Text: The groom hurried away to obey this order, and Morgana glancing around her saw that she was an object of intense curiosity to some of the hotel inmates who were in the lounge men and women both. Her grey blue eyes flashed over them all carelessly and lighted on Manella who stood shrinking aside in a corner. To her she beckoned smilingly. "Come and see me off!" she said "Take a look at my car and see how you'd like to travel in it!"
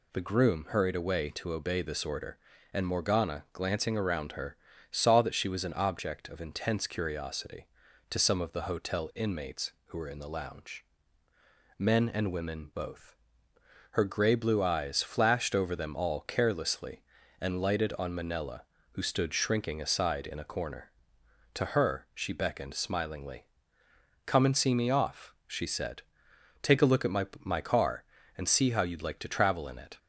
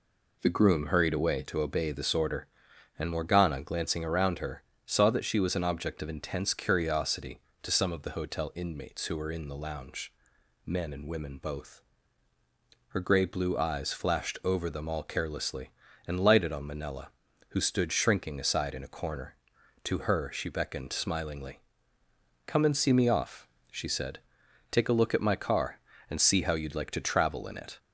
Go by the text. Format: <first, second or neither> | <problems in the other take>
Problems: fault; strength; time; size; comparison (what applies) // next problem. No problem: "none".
second | pauses between "her" and "saw"; slight; at 4.5 s; 0.34 s long; slight in the second // pauses between "lounge" and "men"; noticeable; at 10.8 s; 0.94 s long; noticeable in the second // pauses between "said" and "Take"; noticeable; at 26.0 s; 0.60 s long; noticeable in the second // says "my" twice; at 27.3 s